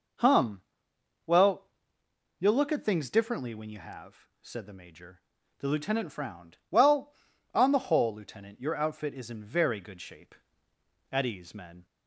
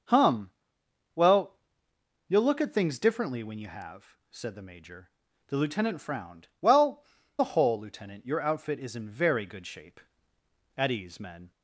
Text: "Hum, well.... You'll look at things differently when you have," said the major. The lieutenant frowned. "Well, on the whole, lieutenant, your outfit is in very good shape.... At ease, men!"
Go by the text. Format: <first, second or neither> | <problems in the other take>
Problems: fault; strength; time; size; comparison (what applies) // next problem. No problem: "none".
first | skips "on"; at 7.2 s